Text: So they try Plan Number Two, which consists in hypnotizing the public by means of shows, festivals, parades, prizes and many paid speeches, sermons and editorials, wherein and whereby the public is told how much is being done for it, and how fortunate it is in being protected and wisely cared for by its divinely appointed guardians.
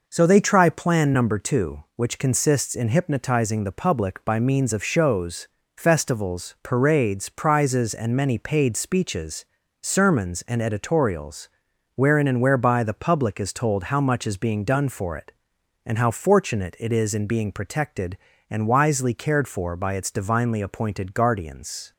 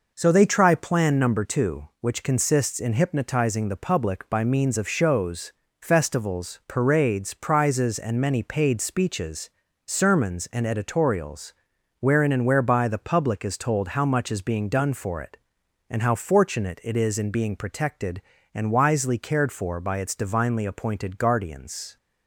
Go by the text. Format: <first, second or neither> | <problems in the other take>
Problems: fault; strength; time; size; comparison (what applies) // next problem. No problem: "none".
neither | none